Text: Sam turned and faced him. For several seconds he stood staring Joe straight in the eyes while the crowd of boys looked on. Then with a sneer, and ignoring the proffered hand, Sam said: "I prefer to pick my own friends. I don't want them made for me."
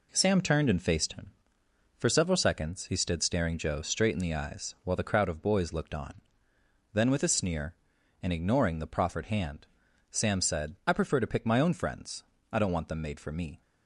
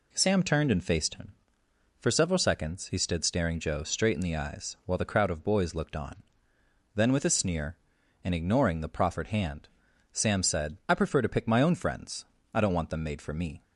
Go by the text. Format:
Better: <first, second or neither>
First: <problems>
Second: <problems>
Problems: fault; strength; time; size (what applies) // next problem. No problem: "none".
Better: second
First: gets quieter; noticeable; throughout; 6 dB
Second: none